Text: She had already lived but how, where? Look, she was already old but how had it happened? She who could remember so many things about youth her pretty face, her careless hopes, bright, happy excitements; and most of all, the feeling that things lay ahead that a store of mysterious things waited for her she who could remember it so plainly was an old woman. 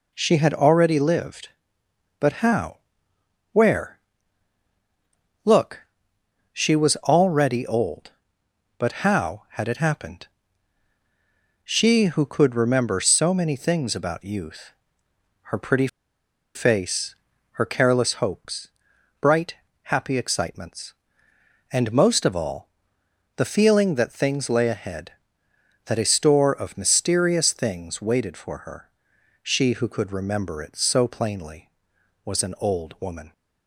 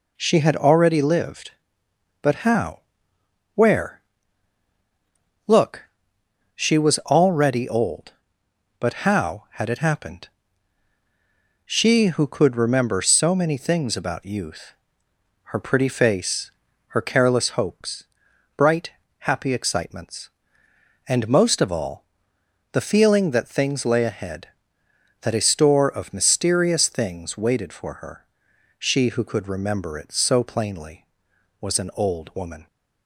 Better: second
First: pauses between "youth" and "her"; noticeable; at 14.7 s; 0.74 s long // pauses between "pretty" and "face"; noticeable; at 15.8 s; 0.68 s long // pauses between "her" and "she"; noticeable; at 28.8 s; 0.54 s long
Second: pauses between "youth" and "her"; noticeable; at 14.7 s; 0.74 s long // pauses between "her" and "she"; noticeable; at 28.2 s; 0.54 s long

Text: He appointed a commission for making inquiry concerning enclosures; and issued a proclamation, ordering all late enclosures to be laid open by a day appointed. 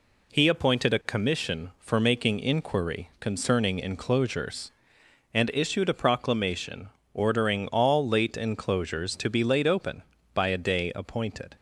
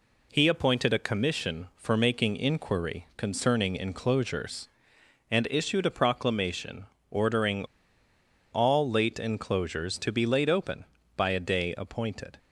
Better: first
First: none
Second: pauses between "ordering" and "all"; noticeable; at 7.6 s; 0.87 s long

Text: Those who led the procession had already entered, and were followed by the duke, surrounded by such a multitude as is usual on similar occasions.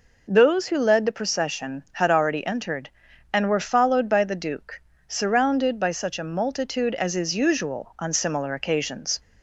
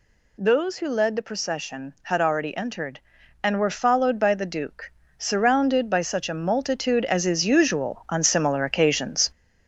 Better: first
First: none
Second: gets louder; noticeable; throughout; 4.5 dB

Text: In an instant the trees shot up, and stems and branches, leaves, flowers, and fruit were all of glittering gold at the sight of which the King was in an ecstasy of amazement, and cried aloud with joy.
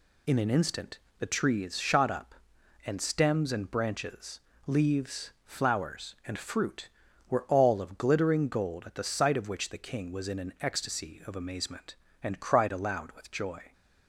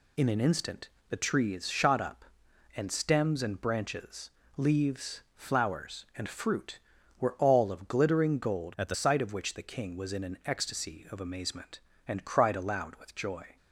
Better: first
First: pauses between "instant" and "the"; slight; at 0.9 s; 0.18 s long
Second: pauses between "instant" and "the"; slight; at 0.8 s; 0.18 s long // changes voice from "at" to "the"; from 8.7 to 8.9 s; 0.2 s long

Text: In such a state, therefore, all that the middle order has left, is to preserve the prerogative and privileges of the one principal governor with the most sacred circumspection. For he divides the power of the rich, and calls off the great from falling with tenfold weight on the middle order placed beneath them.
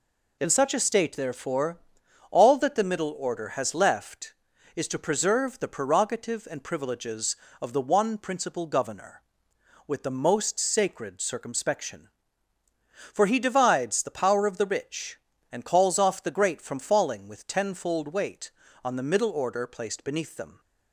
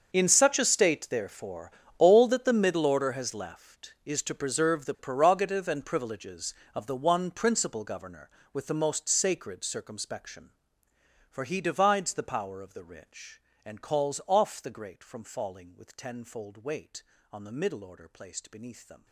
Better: first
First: none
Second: gets quieter; strong; throughout; 18 dB

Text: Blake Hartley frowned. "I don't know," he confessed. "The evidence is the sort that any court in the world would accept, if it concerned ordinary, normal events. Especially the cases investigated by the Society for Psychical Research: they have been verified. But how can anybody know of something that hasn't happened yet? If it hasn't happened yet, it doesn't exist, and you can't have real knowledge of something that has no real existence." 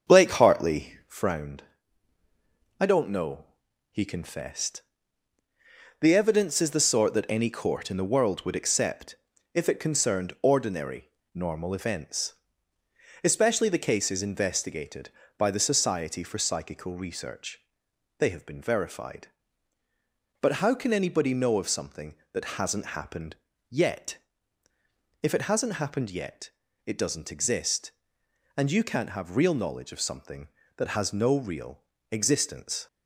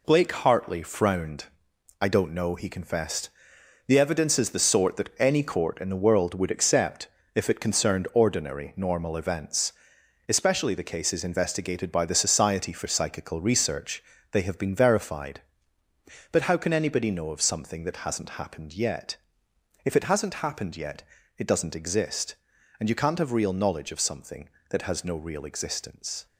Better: second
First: starts louder than the rest; until 1.3 s; 6.5 dB // pauses between "happened" and "yet"; slight; at 23.3 s; 0.34 s long // pauses between "real" and "existence"; slight; at 31.8 s; 0.28 s long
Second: none

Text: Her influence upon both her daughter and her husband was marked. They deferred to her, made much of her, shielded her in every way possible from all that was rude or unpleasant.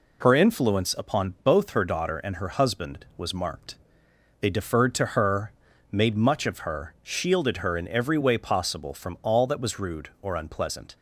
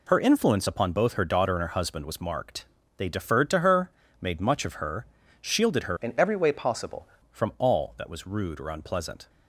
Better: first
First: none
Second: changes voice from "in" to "possible"; from 6.0 to 7.0 s; 1.0 s long

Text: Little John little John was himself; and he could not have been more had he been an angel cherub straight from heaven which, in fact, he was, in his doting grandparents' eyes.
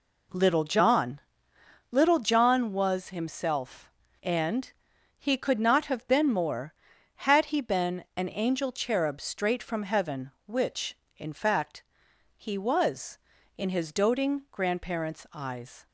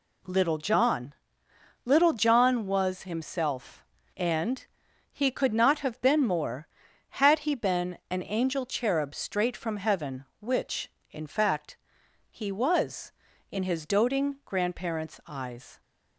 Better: second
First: starts louder than the rest; until 1.8 s; 3.5 dB // pauses between "John" and "little"; noticeable; at 1.2 s; 0.68 s long // pauses between "and" and "he"; noticeable; at 4.7 s; 0.46 s long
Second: pauses between "John" and "little"; noticeable; at 1.1 s; 0.68 s long // pauses between "and" and "he"; noticeable; at 4.6 s; 0.46 s long

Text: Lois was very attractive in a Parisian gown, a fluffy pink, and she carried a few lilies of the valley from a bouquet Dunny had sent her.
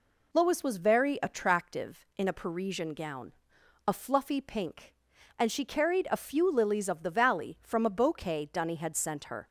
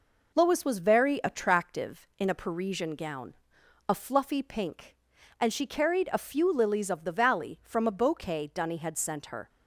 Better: first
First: none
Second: gets quieter; slight; throughout; 3 dB

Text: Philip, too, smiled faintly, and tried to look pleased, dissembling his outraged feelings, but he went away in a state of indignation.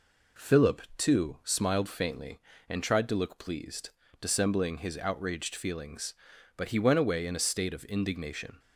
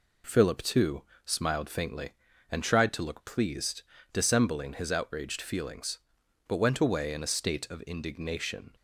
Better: first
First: none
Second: skips "he"; at 6.5 s

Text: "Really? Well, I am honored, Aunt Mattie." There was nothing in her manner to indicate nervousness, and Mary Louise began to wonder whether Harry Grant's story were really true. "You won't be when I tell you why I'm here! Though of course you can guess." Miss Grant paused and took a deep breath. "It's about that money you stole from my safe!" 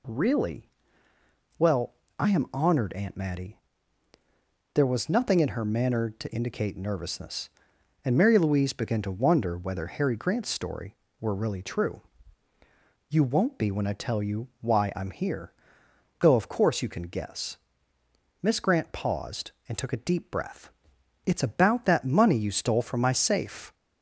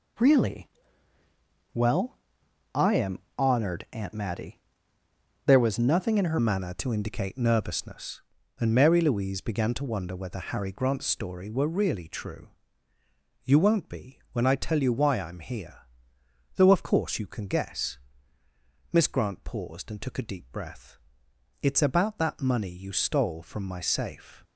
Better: first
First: none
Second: pauses between "am" and "honored"; slight; at 3.1 s; 0.18 s long // changes voice at "manner"; from 6.3 s on; 18.1 s long

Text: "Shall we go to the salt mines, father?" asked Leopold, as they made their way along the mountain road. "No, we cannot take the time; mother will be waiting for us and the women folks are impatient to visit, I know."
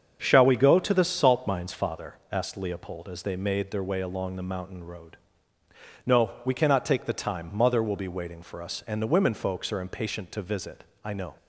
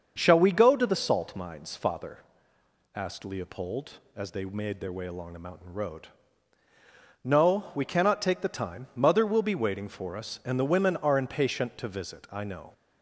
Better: first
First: starts louder than the rest; until 1.2 s; 7 dB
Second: starts louder than the rest; until 1.1 s; 6.5 dB // skips "folks"; at 10.9 s

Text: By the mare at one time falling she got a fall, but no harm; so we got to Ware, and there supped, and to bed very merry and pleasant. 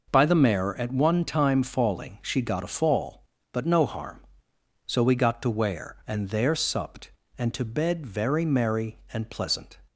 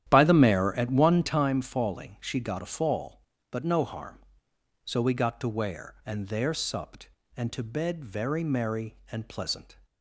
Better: first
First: none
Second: starts louder than the rest; strong; until 1.5 s; 11 dB

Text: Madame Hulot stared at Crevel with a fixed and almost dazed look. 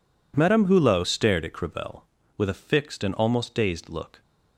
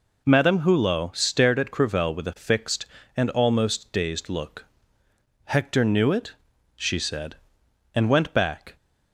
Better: first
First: none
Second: goes on to say "Hector knew it she said And went back"; strong; from 5.4 s on; 3.3 s long

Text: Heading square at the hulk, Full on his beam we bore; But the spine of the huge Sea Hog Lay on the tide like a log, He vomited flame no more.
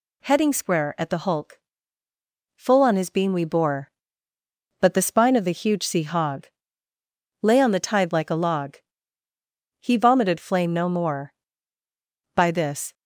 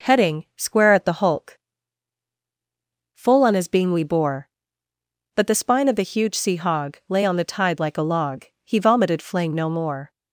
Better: second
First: pauses between "Hog" and "Lay"; noticeable; at 6.4 s; 0.96 s long // goes on to say "By this"; from 12.3 s on; 0.58 s long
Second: none

